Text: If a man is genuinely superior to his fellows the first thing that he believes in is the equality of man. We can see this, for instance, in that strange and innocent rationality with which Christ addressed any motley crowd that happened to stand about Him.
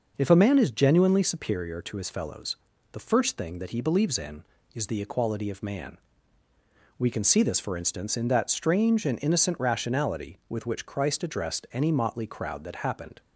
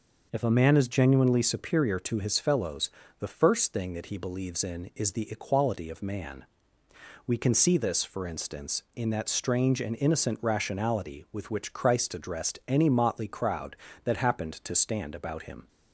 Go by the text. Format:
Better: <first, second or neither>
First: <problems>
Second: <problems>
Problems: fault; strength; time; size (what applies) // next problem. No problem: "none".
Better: second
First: pauses between "fellows" and "the"; slight; at 2.5 s; 0.36 s long // stops before "to stand about Him"; at 13.2 s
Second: pauses between "fellows" and "the"; slight; at 2.8 s; 0.30 s long